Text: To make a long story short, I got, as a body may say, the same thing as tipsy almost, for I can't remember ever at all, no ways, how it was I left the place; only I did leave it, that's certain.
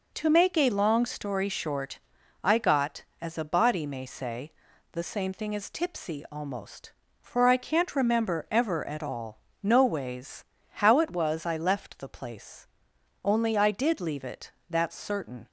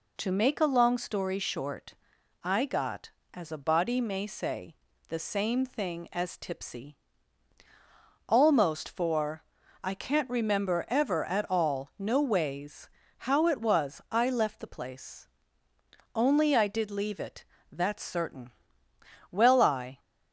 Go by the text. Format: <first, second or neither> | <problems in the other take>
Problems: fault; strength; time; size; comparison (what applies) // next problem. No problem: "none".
first | pauses between "tipsy" and "almost"; strong; at 6.9 s; 1.3 s long // pauses between "for" and "I"; at 9.4 s; 0.44 s long // goes on to say "Well I"; noticeable; from 19.3 s on; 0.68 s long